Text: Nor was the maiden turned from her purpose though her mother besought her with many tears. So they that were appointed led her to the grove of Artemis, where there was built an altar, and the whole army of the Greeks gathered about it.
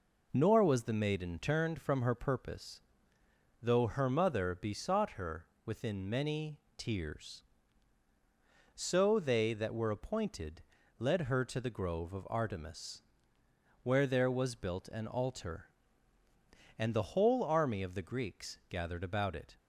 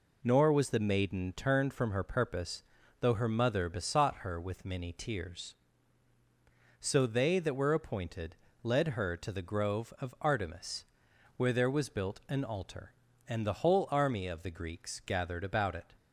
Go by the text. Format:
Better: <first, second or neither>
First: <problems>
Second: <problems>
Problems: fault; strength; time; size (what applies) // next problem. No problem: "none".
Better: second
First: pauses between "purpose" and "though"; noticeable; at 2.8 s; 0.82 s long // says "within" for "with"; at 5.6 s // pauses between "many" and "tears"; slight; at 6.5 s; 0.22 s long // pauses between "appointed" and "led"; slight; at 10.6 s; 0.34 s long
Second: pauses between "purpose" and "though"; at 2.6 s; 0.38 s long // pauses between "appointed" and "led"; slight; at 8.3 s; 0.26 s long